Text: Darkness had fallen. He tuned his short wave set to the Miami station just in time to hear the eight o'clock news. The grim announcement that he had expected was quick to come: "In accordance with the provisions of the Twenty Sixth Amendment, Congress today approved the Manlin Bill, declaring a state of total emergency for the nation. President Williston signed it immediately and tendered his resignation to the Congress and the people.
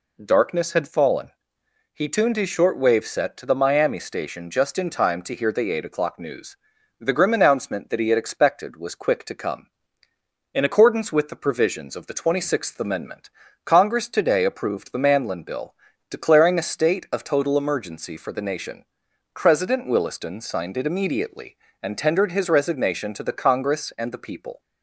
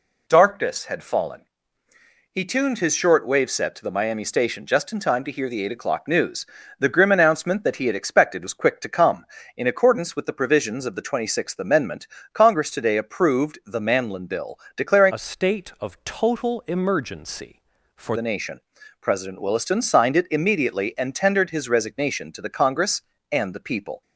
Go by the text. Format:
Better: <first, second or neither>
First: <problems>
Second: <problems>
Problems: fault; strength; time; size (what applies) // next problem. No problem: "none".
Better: first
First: none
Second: changes voice from "a" to "for"; from 15.1 to 18.1 s; 3.0 s long